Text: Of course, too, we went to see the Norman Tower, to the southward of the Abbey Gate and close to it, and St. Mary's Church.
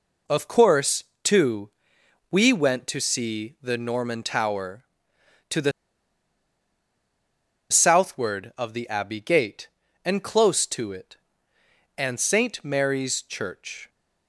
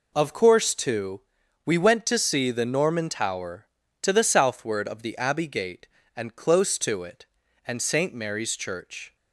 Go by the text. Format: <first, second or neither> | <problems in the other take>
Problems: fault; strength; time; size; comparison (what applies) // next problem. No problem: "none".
second | pauses between "the" and "southward"; strong; at 5.7 s; 1.9 s long